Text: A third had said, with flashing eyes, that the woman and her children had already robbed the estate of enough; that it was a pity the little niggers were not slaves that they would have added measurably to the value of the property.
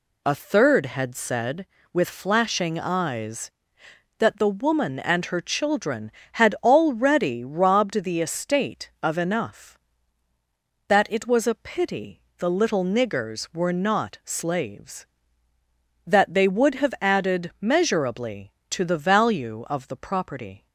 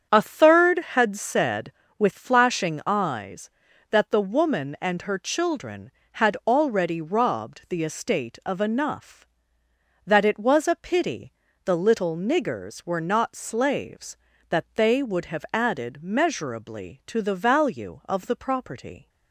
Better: first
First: pauses between "pity" and "the"; slight; at 12.2 s; 0.16 s long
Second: starts louder than the rest; strong; until 1.2 s; 7.5 dB // pauses between "pity" and "the"; slight; at 11.3 s; 0.34 s long

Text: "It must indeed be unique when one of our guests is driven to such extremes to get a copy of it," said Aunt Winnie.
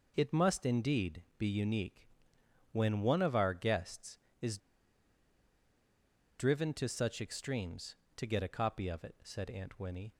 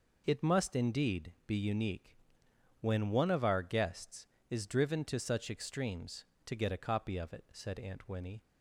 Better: second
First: pauses between "unique" and "when"; noticeable; at 2.0 s; 0.66 s long // pauses between "is" and "driven"; strong; at 4.5 s; 1.7 s long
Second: pauses between "unique" and "when"; noticeable; at 2.1 s; 0.66 s long

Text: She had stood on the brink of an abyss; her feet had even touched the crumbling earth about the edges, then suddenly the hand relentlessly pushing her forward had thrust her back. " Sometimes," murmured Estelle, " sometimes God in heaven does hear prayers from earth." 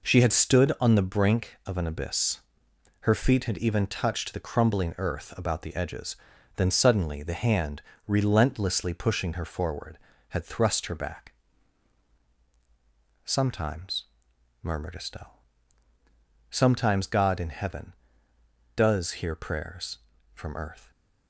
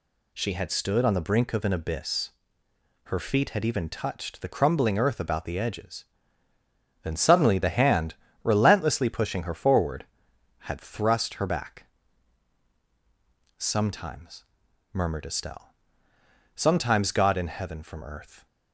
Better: first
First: pauses between "hand" and "relentlessly"; slight; at 7.8 s; 0.26 s long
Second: pauses between "hand" and "relentlessly"; slight; at 8.1 s; 0.28 s long // skips "does hear prayers"; at 17.8 s

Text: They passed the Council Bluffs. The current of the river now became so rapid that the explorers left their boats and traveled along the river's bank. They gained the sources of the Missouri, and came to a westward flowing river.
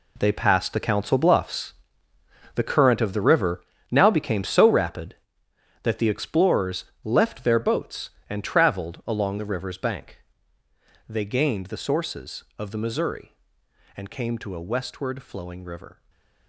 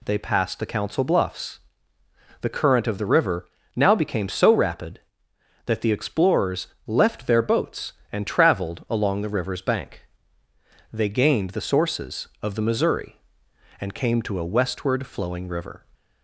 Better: second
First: gets quieter; strong; throughout; 12.5 dB // pauses between "river" and "now"; slight; at 3.6 s; 0.30 s long // pauses between "explorers" and "left"; slight; at 6.8 s; 0.18 s long // stays silent after the last word; slight; from 15.9 s on; 0.5 s long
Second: pauses between "river" and "now"; slight; at 3.4 s; 0.30 s long // pauses between "explorers" and "left"; slight; at 6.6 s; 0.18 s long

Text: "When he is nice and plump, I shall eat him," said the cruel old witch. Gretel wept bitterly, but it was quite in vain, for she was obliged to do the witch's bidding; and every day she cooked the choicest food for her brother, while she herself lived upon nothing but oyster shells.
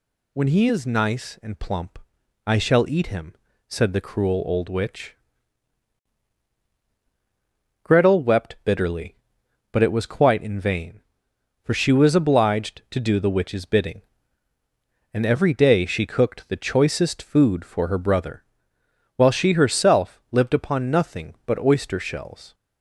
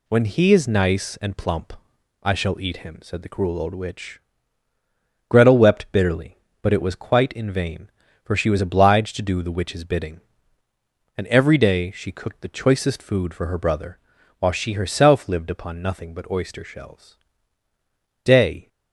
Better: first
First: none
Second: goes on to say "Day"; slight; from 18.2 s on; 0.44 s long

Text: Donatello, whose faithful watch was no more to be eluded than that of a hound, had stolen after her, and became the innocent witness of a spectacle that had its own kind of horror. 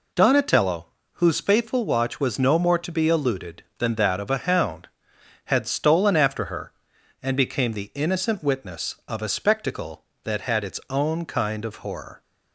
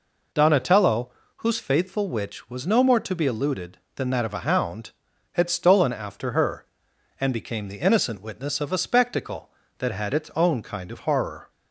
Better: first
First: none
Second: says "witch" for "watch"; at 2.0 s

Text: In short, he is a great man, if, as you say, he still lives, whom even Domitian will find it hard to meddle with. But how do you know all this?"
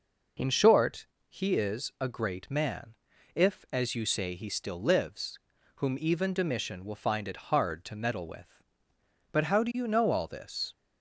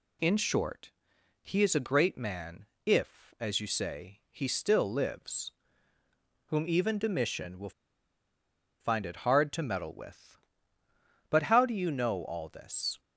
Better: first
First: none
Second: pauses between "will" and "find"; at 7.7 s; 1.0 s long

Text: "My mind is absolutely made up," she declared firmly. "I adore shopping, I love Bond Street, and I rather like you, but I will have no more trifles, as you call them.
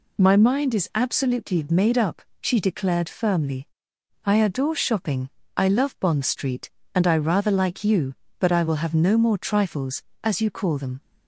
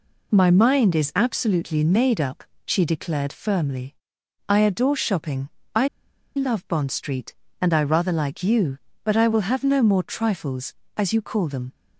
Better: first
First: none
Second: pauses between "I" and "love"; noticeable; at 5.8 s; 0.48 s long

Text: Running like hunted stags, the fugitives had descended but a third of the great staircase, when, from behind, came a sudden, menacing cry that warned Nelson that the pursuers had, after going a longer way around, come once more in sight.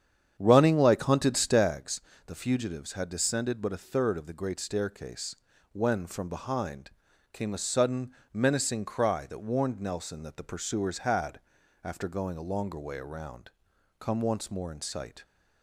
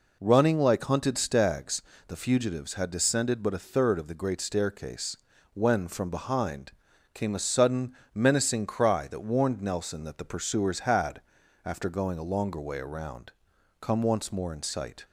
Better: second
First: starts louder than the rest; strong; until 1.7 s; 8.5 dB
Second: none

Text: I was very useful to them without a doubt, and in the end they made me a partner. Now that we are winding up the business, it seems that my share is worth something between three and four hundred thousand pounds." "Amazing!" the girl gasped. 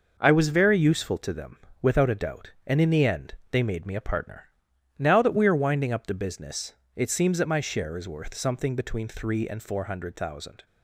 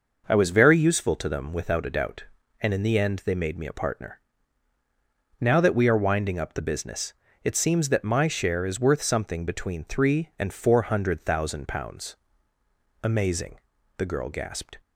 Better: second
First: pauses between "them" and "without"; slight; at 1.5 s; 0.24 s long // pauses between "end" and "they"; slight; at 3.3 s; 0.16 s long // stops before "pounds Amazing the girl gasped"; at 10.6 s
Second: none

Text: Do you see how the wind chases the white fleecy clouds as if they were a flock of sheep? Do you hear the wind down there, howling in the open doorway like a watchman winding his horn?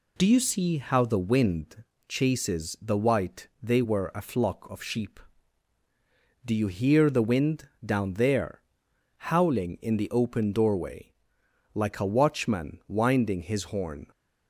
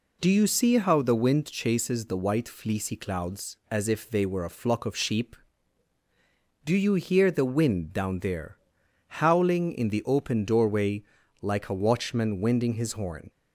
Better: second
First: pauses between "wind" and "chases"; slight; at 1.8 s; 0.26 s long // skips "fleecy clouds as if"; at 3.5 s // pauses between "wind" and "down"; slight; at 7.6 s; 0.16 s long // pauses between "doorway" and "like"; noticeable; at 11.1 s; 0.62 s long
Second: pauses between "doorway" and "like"; slight; at 11.0 s; 0.36 s long

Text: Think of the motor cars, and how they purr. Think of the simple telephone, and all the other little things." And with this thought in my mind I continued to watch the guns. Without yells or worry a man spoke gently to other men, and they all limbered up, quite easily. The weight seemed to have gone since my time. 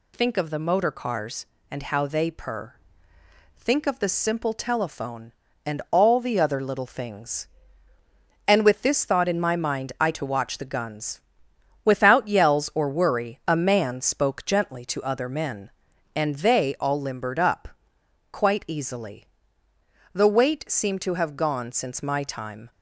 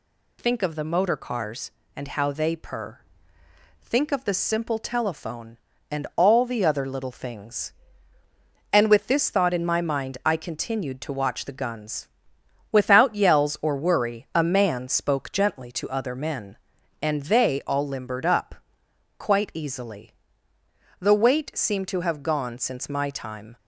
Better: second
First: skips "continued"; at 10.1 s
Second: none

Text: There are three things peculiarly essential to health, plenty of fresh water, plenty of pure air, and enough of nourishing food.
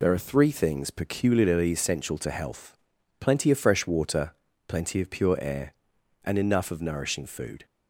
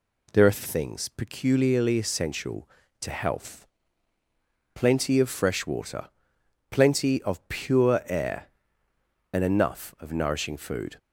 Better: first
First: none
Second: skips "three"; at 0.6 s

